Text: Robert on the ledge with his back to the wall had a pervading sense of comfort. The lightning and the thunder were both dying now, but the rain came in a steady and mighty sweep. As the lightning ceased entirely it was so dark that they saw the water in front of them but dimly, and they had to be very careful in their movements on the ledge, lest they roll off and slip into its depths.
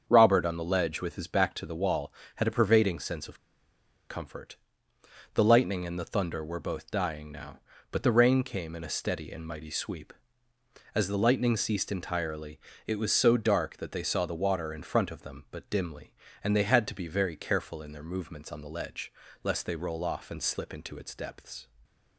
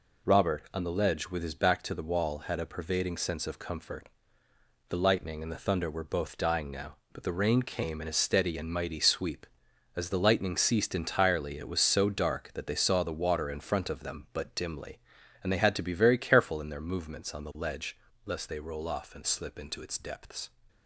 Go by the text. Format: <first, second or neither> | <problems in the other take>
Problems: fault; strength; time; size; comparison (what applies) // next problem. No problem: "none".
second | starts louder than the rest; until 1.0 s; 7 dB // pauses between "of" and "comfort"; noticeable; at 3.3 s; 0.69 s long // pauses between "entirely" and "it"; slight; at 12.5 s; 0.26 s long